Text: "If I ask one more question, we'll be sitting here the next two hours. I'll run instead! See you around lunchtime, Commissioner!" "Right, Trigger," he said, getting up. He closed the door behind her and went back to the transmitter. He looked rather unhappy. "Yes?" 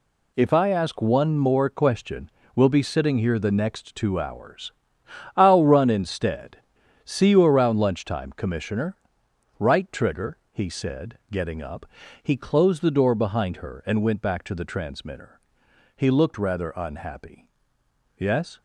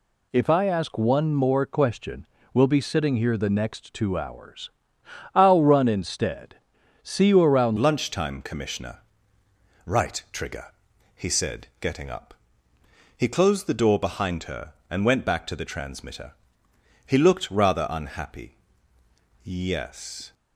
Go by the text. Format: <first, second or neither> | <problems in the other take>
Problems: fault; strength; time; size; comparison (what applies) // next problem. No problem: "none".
first | changes voice at "lunchtime"; from 7.7 s on; 12.6 s long